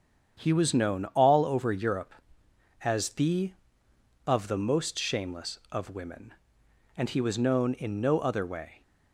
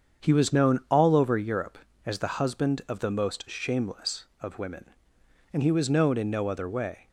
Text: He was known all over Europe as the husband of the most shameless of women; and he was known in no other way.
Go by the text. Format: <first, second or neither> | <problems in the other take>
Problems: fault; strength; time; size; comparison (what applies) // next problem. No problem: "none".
second | starts louder than the rest; strong; until 1.4 s; 8 dB; strong in the second // skips "husband"; at 3.8 s